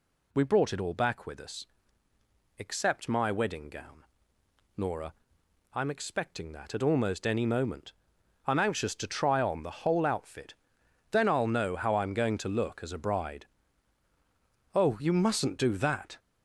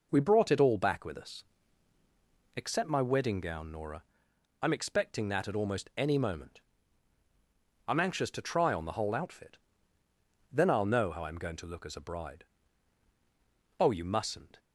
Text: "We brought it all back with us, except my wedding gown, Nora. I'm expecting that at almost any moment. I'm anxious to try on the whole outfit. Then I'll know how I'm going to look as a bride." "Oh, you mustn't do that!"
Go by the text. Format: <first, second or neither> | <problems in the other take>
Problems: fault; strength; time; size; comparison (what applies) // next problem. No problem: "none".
first | stops before "do that"; at 14.5 s